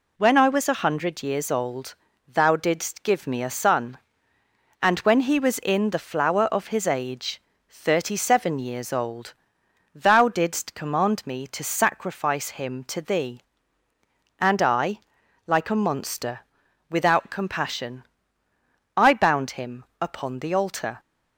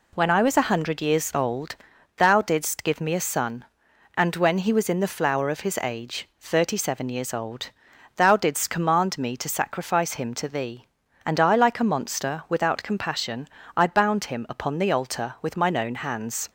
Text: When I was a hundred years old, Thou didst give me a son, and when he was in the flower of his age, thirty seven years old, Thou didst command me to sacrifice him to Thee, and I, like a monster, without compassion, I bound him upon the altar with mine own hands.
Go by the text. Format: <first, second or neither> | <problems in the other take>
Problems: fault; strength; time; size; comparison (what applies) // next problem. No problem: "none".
second | pauses between "him" and "upon"; slight; at 19.8 s; 0.16 s long // stops before "with mine own hands"; at 20.9 s